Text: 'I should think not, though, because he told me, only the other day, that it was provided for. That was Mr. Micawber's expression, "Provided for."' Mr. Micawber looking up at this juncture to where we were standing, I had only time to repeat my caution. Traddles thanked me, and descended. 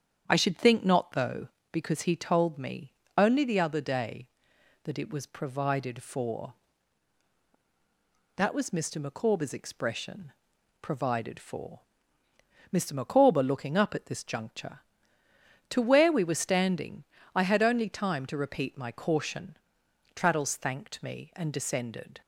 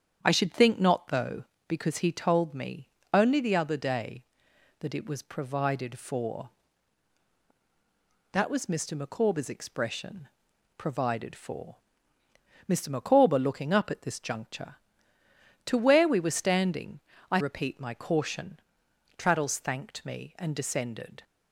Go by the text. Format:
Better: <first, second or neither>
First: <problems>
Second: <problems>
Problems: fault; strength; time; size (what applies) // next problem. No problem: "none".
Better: first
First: starts louder than the rest; strong; until 1.2 s; 8.5 dB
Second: starts louder than the rest; strong; until 1.2 s; 8 dB // skips "had only time to"; at 17.3 s